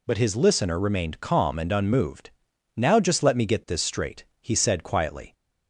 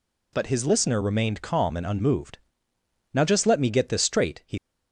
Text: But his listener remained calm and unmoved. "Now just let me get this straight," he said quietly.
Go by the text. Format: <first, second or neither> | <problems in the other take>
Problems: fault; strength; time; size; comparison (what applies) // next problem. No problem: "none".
first | stops before "said quietly"; at 4.5 s